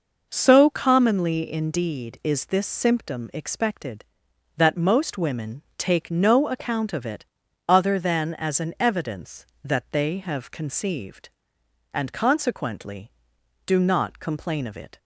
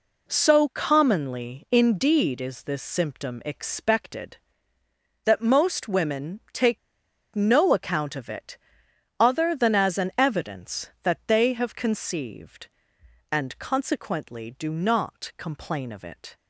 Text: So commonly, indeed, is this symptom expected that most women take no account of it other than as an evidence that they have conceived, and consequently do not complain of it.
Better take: first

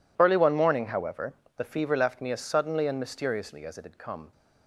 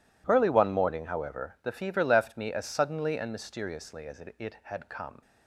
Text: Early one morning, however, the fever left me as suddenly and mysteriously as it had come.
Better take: first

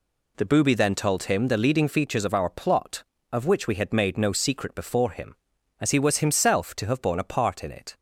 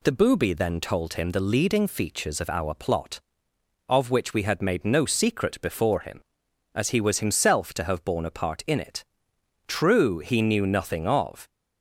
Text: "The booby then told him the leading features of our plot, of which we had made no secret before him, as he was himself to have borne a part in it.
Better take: first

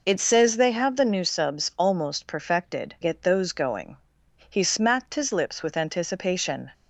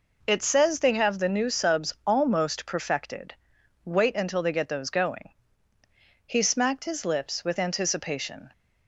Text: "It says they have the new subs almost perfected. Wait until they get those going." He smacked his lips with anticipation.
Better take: second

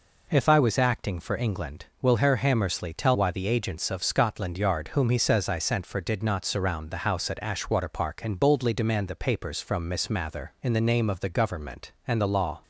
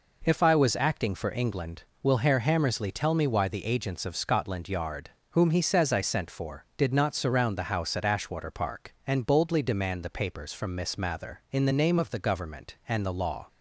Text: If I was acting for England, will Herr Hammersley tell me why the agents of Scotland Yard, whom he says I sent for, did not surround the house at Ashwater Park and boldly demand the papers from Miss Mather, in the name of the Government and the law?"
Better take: second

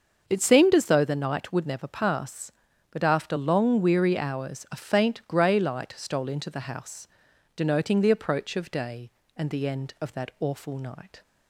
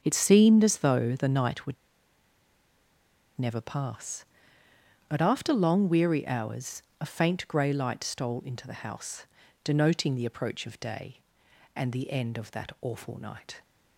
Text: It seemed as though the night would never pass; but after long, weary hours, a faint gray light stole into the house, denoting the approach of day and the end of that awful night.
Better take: first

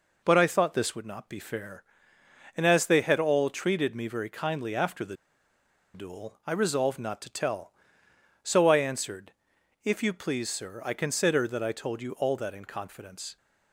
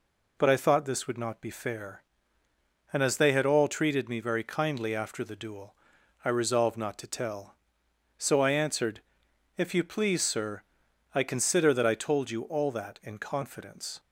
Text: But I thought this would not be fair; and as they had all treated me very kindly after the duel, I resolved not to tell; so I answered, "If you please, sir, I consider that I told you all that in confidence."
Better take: second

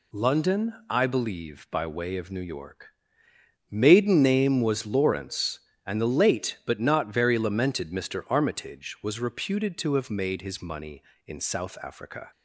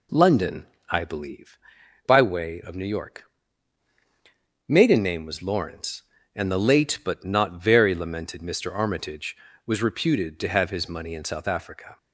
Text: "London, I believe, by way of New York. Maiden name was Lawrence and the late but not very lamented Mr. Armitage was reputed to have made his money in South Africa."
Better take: first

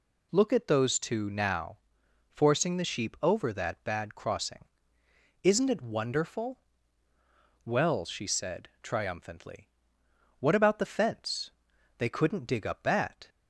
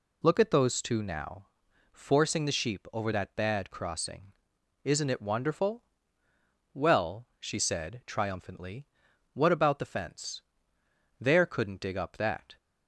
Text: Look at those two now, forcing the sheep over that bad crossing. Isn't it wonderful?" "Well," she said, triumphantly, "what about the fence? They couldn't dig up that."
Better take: first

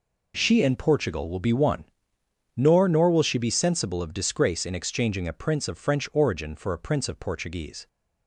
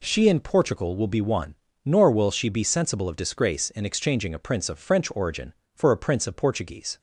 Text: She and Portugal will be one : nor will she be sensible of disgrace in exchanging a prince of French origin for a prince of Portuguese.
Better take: second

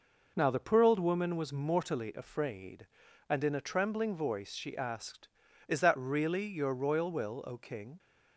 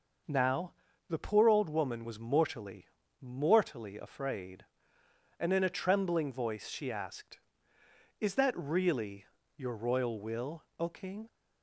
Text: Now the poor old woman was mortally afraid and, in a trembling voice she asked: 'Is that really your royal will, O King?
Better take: first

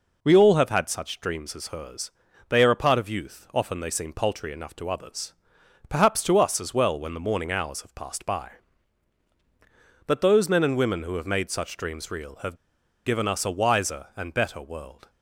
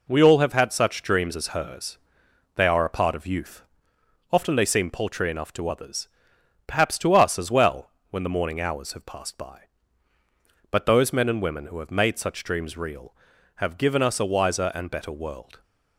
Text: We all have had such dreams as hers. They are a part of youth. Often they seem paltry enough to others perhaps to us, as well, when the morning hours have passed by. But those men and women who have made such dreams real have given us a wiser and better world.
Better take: second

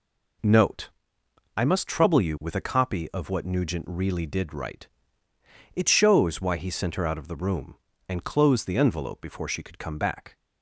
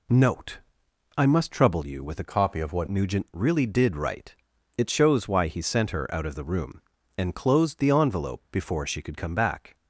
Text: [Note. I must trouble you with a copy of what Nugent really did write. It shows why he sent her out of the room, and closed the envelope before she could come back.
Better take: first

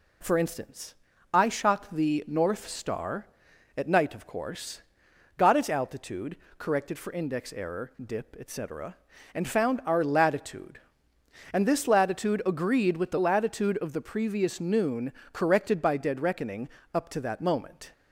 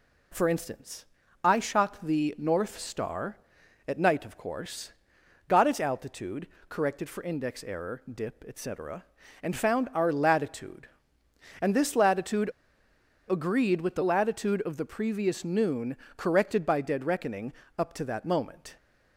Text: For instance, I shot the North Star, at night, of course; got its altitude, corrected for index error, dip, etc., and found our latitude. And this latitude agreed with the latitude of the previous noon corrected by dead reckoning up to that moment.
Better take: first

